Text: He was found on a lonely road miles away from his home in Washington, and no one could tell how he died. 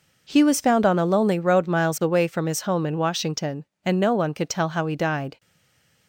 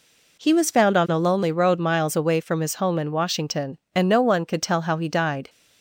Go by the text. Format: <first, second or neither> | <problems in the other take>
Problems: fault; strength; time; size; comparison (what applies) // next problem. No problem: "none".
second | stays silent after the last word; slight; from 5.3 s on; 0.7 s long